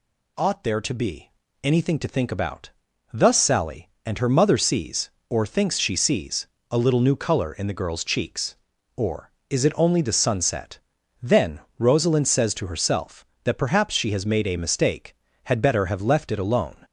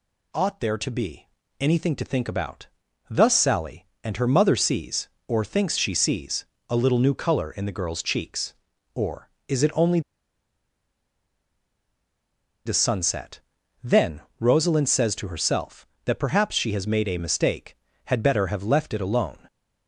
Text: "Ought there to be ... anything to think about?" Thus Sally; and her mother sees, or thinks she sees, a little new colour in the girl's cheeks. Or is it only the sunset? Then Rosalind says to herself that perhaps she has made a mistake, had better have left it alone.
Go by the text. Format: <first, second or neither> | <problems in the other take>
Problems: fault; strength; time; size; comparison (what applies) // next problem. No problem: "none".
first | pauses between "only" and "the"; strong; at 9.9 s; 2.6 s long // pauses between "Then" and "Rosalind"; slight; at 14.2 s; 0.18 s long; slight in the first